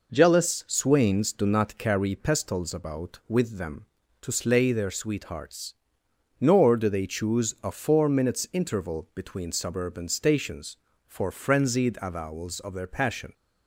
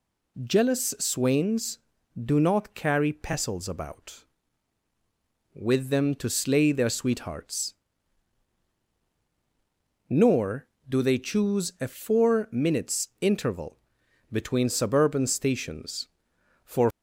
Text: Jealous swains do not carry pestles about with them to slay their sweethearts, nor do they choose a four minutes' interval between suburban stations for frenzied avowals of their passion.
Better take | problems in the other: first | pauses between "interval" and "between"; noticeable; at 13.7 s; 0.52 s long // stops before "frenzied avowals of their passion"; at 16.8 s

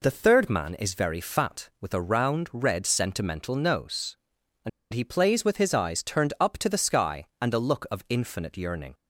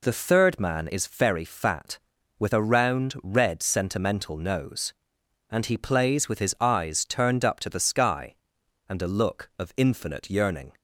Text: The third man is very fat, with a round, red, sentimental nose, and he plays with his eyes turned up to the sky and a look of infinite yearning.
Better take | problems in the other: second | pauses between "and" and "he"; slight; at 4.6 s; 0.24 s long

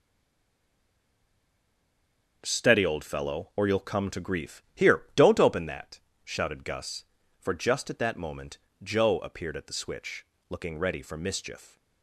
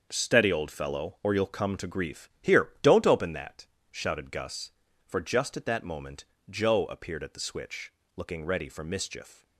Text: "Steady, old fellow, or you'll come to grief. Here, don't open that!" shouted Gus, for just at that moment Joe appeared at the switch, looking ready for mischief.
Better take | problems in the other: second | stays silent before the first word; until 2.4 s; 2.4 s long // starts louder than the rest; until 3.4 s; 6.5 dB; also in the second // pauses between "moment" and "Joe"; slight; at 8.5 s; 0.26 s long; slight in the second

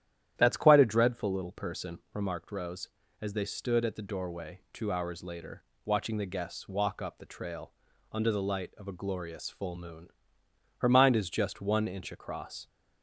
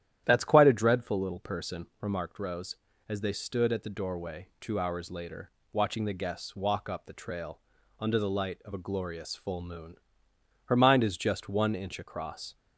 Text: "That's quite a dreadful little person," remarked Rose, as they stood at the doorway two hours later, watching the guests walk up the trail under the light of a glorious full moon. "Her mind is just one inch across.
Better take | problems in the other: neither | starts louder than the rest; strong; the same in both // pauses between "trail" and "under"; the same in both

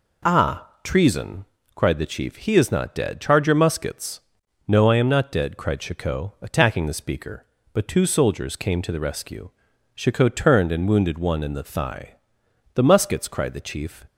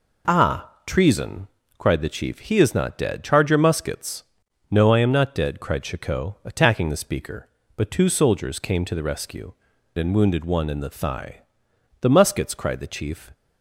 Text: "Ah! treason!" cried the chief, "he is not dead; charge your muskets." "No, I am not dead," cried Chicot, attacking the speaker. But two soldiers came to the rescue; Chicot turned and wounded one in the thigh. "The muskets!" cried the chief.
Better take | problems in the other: first | skips "Chicot turned"; at 9.7 s

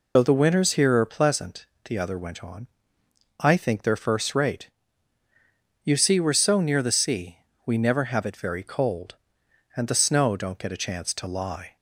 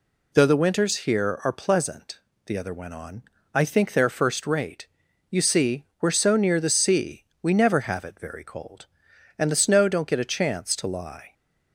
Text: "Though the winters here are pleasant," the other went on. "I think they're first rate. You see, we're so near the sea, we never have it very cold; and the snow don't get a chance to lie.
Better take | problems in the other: second | loses the start of "Though"; at 0.1 s; 65 ms

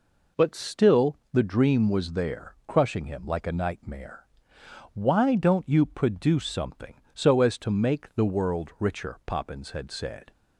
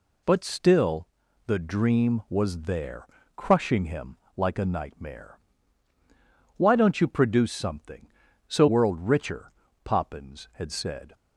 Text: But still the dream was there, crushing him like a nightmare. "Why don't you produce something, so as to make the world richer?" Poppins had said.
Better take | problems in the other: first | pauses between "still" and "the"; at 1.0 s; 0.40 s long; slight in the first // pauses between "him" and "like"; slight; at 4.1 s; 0.20 s long // skips "as to make the"; at 8.6 s

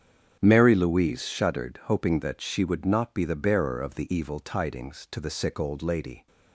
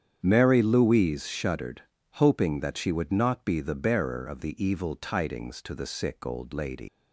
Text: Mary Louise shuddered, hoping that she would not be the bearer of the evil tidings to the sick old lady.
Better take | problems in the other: first | starts louder than the rest; strong; until 1.2 s; 8.5 dB; strong in the first // leaves "lady" unfinished; at 6.8 s; 135 ms

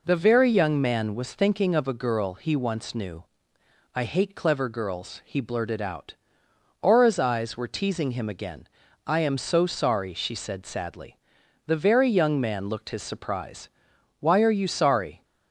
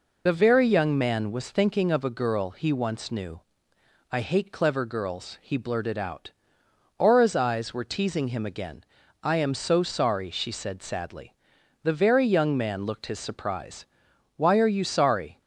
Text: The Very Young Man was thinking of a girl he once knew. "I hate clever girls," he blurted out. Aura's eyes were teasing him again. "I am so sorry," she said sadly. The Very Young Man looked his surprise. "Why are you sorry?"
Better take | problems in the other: first | loses the start of "The"; at 0.2 s; 30 ms

